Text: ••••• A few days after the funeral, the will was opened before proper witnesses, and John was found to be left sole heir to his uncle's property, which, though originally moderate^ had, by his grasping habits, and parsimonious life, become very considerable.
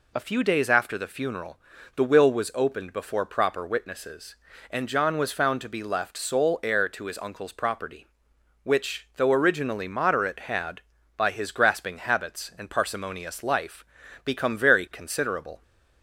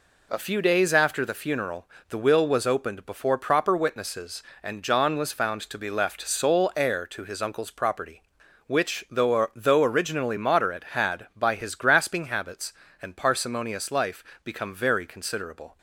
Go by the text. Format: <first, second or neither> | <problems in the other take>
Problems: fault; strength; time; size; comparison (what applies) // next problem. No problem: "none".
first | says "though" twice; at 9.5 s